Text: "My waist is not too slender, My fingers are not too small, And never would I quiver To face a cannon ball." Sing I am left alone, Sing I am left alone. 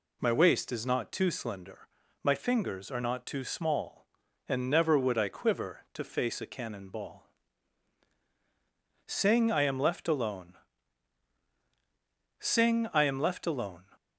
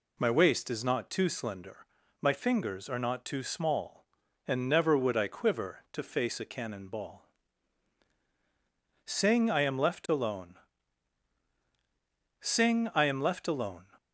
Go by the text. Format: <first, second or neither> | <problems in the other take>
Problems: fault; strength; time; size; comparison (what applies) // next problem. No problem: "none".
neither | none